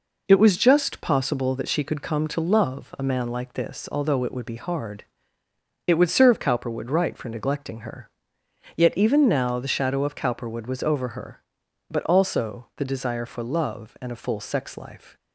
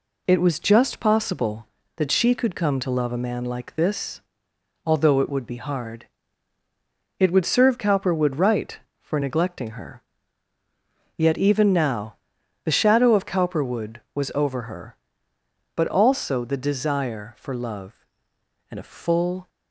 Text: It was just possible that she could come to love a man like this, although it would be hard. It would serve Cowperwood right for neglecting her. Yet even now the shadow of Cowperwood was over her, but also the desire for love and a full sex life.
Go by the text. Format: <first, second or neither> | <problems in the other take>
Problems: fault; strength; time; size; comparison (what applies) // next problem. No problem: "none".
first | pauses between "now" and "the"; noticeable; at 12.1 s; 0.48 s long // stops before "sex life"; at 19.4 s